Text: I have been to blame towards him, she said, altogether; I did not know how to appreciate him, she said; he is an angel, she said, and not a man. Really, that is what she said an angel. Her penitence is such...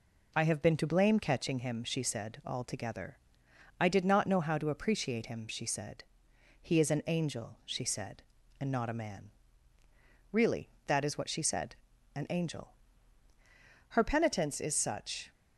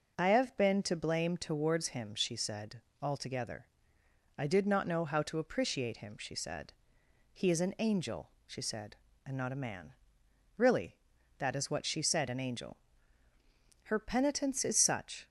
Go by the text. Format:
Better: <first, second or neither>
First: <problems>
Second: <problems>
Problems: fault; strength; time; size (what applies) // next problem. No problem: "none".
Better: second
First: says "catching" for "towards"; at 1.1 s // pauses between "said" and "an"; at 11.7 s; 0.40 s long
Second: none